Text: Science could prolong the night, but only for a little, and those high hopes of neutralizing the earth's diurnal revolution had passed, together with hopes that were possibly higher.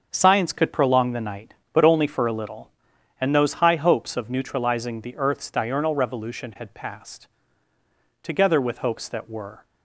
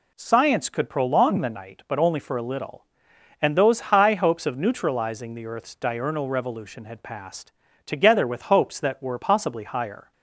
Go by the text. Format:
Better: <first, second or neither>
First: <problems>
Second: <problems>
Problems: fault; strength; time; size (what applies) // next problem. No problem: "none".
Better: second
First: starts louder than the rest; until 1.1 s; 6.5 dB // stops before "possibly higher"; at 9.6 s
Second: none